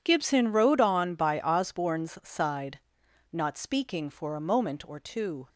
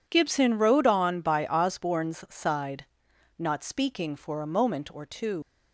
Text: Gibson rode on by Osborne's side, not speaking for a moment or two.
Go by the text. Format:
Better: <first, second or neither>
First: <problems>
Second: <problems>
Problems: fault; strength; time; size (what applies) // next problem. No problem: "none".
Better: first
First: none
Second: leaves "two" unfinished; at 5.4 s; 120 ms